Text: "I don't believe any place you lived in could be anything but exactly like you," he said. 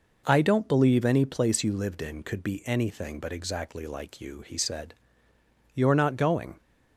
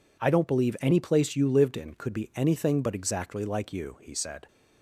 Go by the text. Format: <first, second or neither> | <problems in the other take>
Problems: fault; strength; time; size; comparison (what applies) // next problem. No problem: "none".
second | goes on to say "You're not going"; noticeable; from 5.7 s on; 0.86 s long